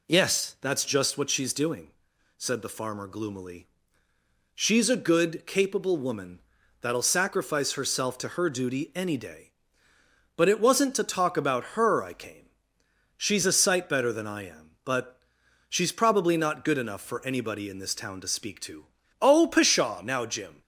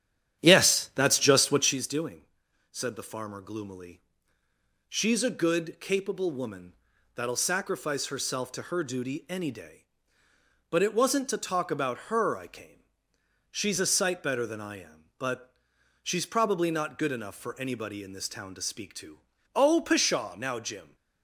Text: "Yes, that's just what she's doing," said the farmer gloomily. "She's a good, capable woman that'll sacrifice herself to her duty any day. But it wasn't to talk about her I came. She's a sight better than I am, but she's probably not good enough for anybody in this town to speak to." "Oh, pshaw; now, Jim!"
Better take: first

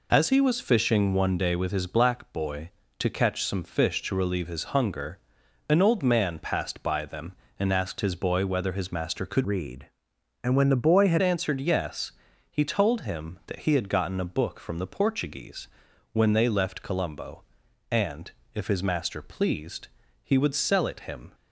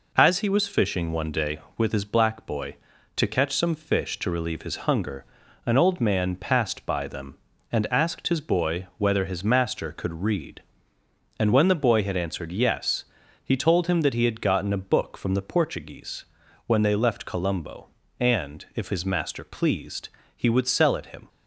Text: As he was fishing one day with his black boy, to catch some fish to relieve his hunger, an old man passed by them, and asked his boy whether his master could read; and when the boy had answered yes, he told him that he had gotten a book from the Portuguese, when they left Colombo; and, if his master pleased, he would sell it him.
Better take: second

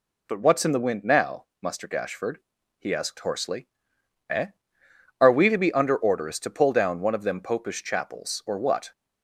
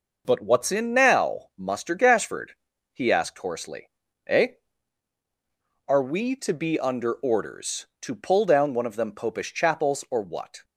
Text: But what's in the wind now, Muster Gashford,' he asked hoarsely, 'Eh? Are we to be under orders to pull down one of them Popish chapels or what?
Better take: first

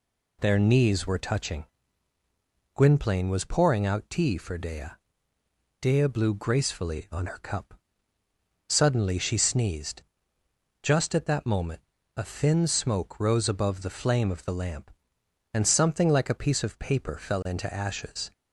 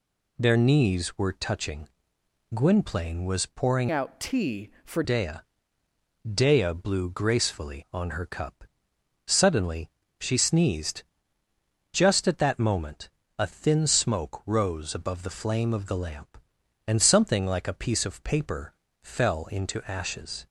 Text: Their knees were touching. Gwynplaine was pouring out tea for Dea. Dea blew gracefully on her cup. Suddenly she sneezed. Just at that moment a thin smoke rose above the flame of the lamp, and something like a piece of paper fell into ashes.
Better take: first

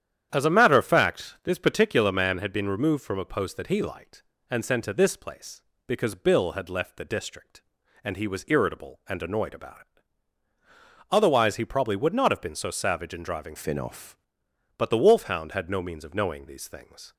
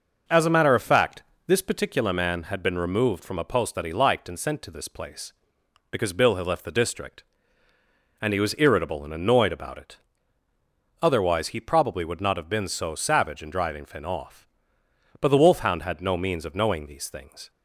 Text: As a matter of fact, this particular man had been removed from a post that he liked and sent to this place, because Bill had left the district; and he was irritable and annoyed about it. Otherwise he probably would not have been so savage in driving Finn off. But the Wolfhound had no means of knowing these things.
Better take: second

